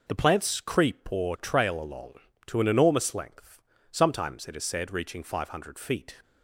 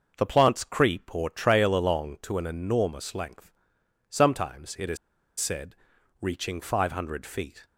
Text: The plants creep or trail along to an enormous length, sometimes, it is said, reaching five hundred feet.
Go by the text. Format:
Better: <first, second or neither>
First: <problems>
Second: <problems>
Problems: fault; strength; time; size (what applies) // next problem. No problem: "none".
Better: first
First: none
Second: pauses between "is" and "said"; at 4.9 s; 0.43 s long